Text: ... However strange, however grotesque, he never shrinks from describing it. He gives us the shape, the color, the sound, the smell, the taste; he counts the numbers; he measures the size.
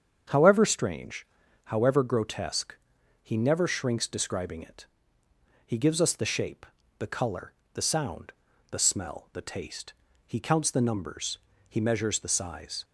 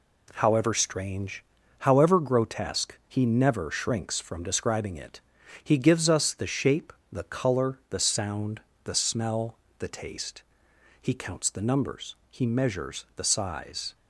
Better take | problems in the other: second | starts louder than the rest; strong; until 1.6 s; 8 dB // skips "from"; at 4.0 s

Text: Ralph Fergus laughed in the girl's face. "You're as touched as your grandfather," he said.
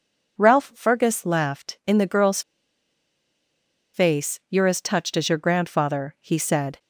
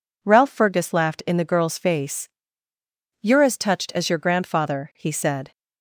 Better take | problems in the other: second | pauses between "girl's" and "face"; strong; at 2.4 s; 1.5 s long

